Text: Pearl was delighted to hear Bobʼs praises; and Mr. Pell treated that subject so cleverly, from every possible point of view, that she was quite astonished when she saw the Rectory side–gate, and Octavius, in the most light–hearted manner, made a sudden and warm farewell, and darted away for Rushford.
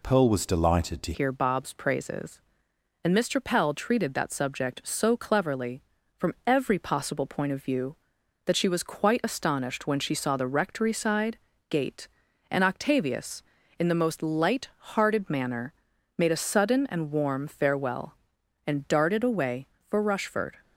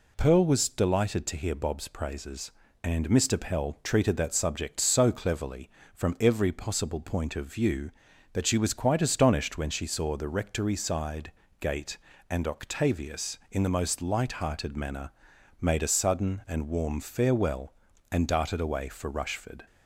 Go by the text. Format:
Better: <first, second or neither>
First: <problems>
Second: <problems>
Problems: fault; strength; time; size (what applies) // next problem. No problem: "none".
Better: second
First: changes voice at "hear"; from 1.1 s on; 19.4 s long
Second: none